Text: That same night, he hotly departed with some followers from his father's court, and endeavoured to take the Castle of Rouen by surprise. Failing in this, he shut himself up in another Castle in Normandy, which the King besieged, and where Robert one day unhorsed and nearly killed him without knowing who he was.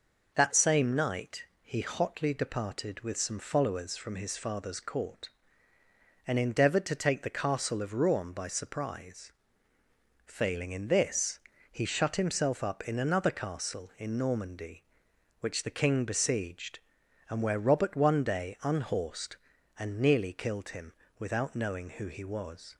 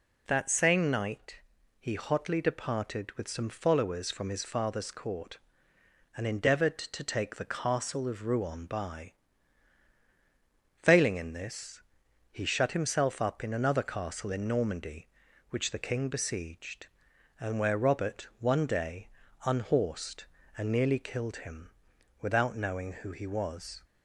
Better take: first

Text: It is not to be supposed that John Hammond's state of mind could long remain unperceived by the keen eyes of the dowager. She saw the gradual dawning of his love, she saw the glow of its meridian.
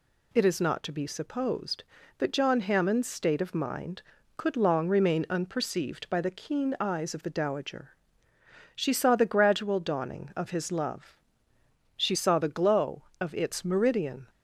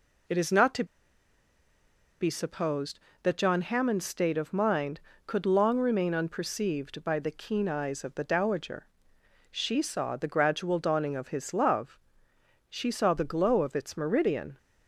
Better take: first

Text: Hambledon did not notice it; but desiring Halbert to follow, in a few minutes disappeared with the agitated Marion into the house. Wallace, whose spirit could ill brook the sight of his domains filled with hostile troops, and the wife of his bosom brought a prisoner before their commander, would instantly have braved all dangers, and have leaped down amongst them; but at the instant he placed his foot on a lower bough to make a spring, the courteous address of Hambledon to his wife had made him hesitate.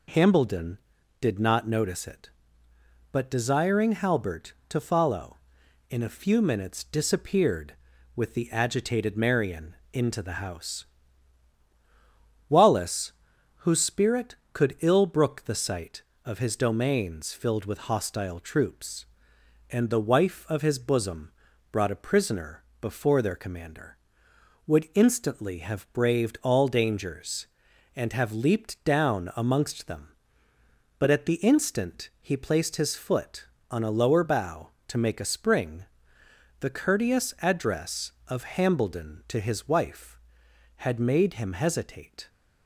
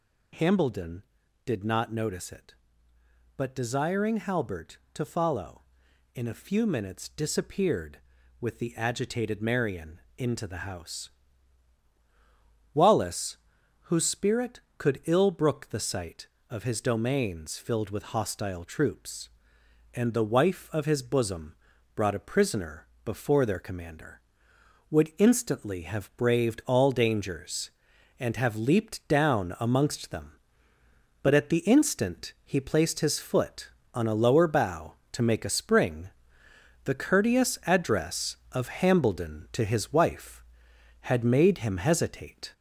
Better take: first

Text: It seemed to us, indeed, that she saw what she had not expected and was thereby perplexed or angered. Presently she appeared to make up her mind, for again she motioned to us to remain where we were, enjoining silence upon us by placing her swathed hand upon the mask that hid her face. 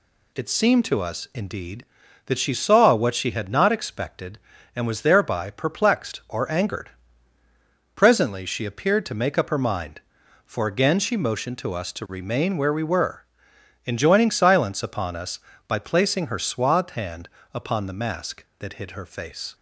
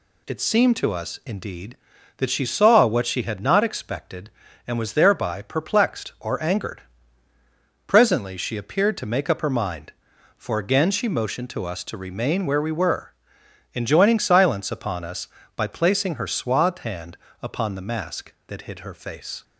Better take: neither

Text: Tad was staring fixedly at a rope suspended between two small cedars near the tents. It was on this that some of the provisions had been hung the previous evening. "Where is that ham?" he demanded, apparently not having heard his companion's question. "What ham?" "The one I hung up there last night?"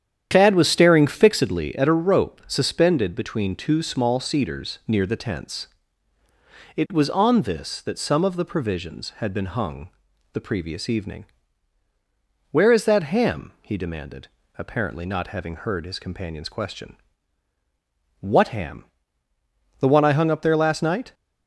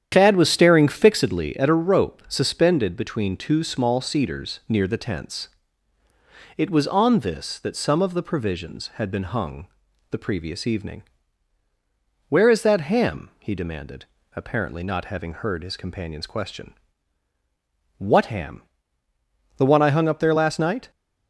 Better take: neither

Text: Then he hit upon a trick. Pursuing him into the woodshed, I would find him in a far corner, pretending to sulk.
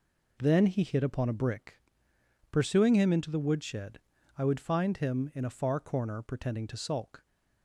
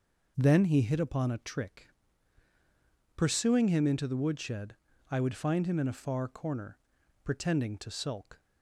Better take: second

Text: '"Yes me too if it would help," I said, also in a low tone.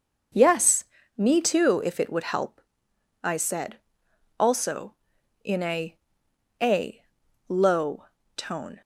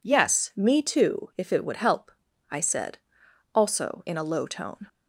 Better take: second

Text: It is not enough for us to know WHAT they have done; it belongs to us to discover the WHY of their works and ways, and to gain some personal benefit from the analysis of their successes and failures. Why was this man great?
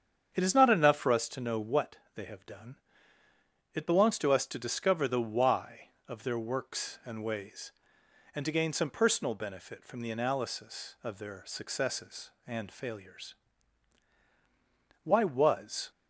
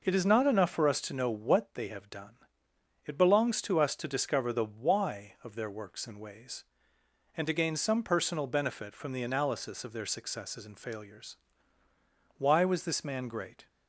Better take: second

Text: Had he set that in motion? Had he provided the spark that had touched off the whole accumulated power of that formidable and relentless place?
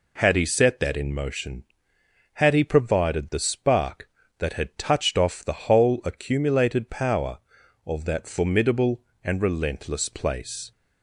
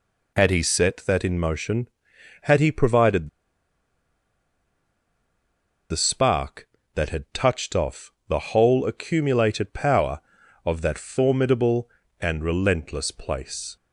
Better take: first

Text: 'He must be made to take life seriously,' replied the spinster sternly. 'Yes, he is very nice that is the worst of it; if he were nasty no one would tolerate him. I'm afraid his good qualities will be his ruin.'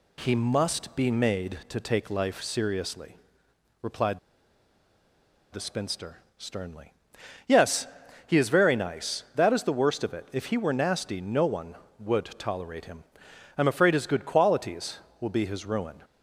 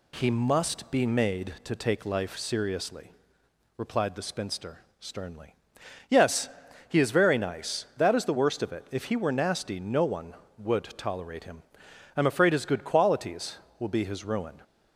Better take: second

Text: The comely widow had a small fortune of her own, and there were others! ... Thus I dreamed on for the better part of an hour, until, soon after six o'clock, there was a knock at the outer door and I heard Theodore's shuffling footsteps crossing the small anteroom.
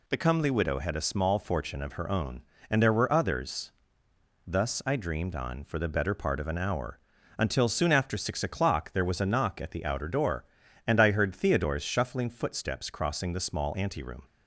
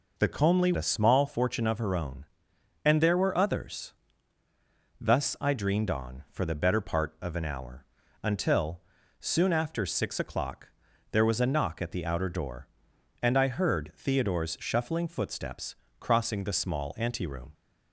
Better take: first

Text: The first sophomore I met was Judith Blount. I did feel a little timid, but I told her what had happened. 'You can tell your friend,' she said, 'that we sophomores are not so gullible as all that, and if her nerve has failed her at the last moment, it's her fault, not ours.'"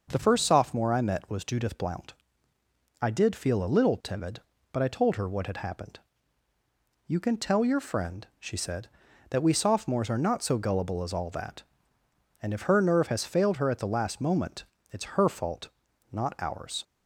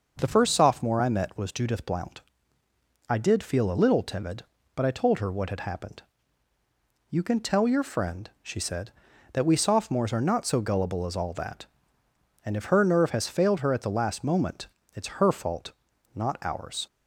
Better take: neither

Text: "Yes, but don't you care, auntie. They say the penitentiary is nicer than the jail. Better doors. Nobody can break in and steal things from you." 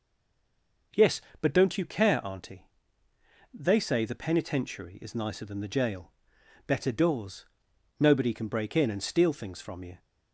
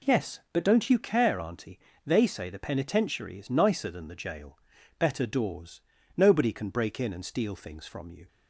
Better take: second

